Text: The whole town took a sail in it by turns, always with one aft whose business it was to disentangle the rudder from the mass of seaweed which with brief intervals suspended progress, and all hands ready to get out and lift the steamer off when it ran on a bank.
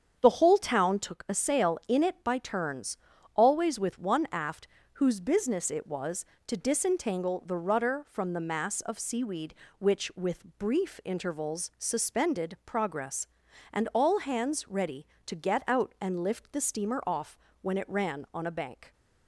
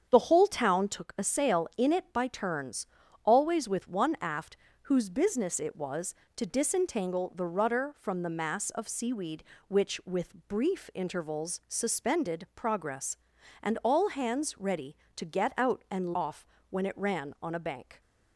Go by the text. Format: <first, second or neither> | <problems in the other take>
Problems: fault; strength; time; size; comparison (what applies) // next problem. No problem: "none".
first | starts louder than the rest; strong; until 1.1 s; 8 dB; strong in the first // pauses between "aft" and "whose"; slight; at 4.5 s; 0.28 s long; slight in the first // skips "lift the steamer"; at 16.1 s // pauses between "off" and "when"; slight; at 16.4 s; 0.24 s long; slight in the first